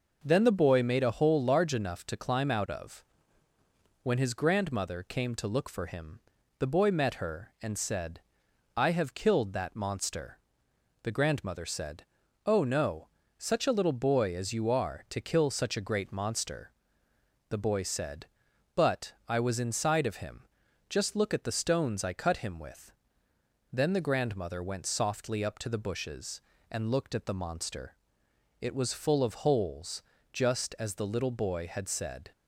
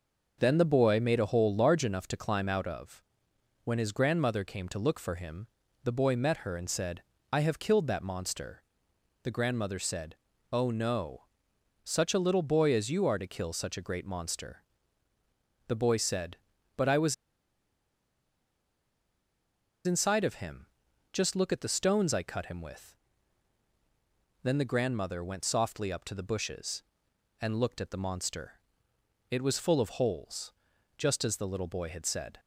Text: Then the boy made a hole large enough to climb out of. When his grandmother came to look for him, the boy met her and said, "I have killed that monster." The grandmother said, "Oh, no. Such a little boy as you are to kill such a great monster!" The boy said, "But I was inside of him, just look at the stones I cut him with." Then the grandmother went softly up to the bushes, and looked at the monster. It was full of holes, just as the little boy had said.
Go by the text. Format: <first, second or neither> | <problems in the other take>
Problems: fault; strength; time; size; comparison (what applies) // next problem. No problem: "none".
first | pauses between "was" and "inside"; strong; at 17.1 s; 2.7 s long